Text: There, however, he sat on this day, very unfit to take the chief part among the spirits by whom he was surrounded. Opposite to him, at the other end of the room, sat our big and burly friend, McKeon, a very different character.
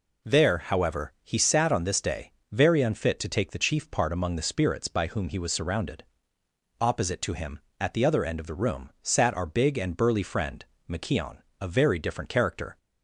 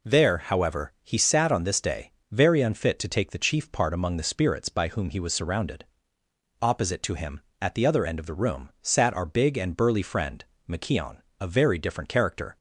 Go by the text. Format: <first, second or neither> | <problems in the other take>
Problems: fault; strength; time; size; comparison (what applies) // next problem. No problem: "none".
neither | none